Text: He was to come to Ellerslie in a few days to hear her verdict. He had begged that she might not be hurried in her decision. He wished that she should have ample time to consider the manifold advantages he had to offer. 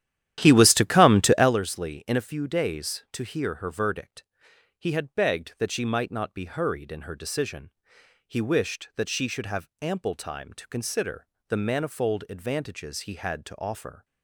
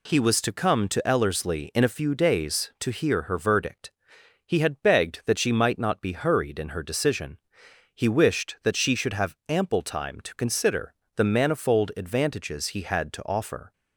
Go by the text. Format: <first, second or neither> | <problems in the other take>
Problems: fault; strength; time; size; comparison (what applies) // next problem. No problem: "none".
second | starts louder than the rest; strong; until 1.6 s; 12 dB // pauses between "consider" and "the"; slight; at 11.2 s; 0.22 s long; slight in the second